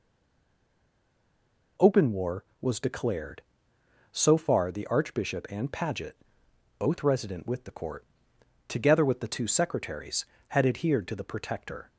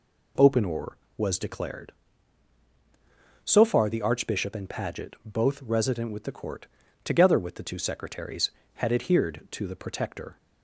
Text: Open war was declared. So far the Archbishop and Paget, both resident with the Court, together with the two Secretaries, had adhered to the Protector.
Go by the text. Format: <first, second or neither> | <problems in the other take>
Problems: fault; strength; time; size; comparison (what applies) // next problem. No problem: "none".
second | stays silent before the first word; noticeable; until 1.7 s; 1.7 s long